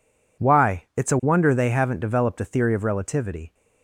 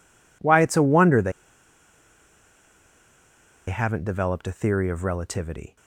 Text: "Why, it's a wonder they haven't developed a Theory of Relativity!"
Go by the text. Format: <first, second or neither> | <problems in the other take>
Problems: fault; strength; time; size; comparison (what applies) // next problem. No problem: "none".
first | pauses between "they" and "haven't"; strong; at 1.3 s; 2.3 s long